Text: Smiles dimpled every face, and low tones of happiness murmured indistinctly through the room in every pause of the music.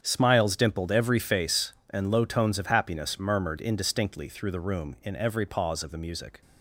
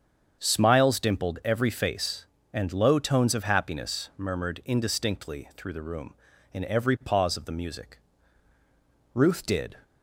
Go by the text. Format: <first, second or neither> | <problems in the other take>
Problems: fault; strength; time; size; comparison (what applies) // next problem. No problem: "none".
first | starts louder than the rest; strong; until 1.4 s; 7 dB; strong in the first // goes on to say "Ruth did"; noticeable; from 9.1 s on; 0.62 s long